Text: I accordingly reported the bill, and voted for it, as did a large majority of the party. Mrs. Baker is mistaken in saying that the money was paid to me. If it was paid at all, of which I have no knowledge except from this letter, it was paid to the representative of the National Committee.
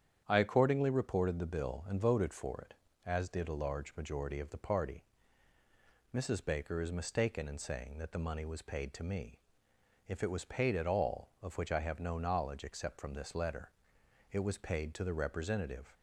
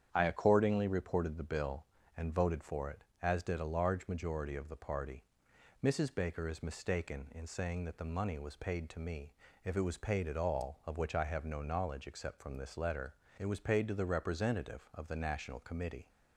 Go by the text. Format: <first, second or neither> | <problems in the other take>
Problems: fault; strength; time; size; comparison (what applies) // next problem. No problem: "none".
second | starts louder than the rest; strong; until 1.2 s; 9 dB; strong in the second // stops before "of the National Committee"; at 15.9 s